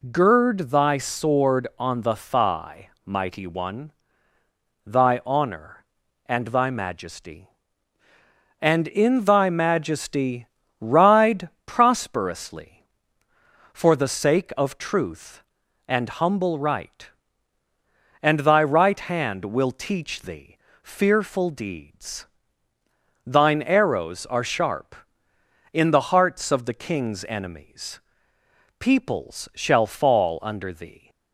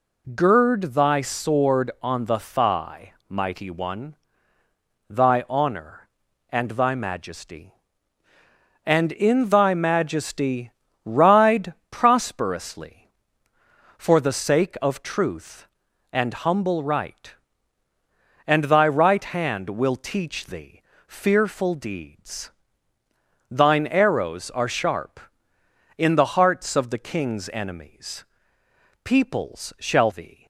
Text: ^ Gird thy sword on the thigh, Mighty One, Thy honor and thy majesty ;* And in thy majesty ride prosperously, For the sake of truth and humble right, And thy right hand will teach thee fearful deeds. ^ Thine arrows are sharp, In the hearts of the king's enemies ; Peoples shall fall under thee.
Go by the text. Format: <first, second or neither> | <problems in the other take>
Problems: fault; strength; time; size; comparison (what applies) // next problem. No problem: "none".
first | pauses between "majesty" and "ride"; slight; at 10.7 s; 0.32 s long; slight in the first // pauses between "ride" and "prosperously"; slight; at 11.7 s; 0.18 s long; slight in the first // pauses between "thee" and "fearful"; slight; at 20.8 s; 0.24 s long; slight in the first // skips "fall under"; at 30.1 s